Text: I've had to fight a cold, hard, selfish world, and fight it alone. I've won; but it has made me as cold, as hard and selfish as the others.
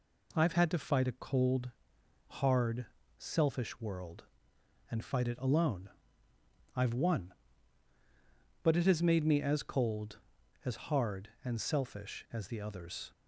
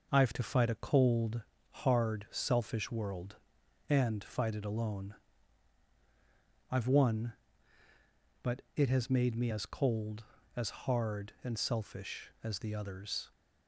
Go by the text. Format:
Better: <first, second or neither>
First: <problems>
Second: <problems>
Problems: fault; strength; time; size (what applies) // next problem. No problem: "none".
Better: first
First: none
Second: skips "had"; at 0.3 s